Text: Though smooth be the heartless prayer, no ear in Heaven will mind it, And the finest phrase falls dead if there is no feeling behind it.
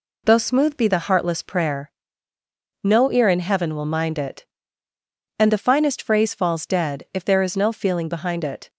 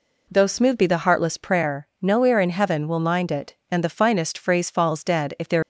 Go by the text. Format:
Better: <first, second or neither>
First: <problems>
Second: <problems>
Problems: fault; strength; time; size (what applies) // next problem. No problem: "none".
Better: first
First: none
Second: stops before "is no feeling behind it"; at 5.6 s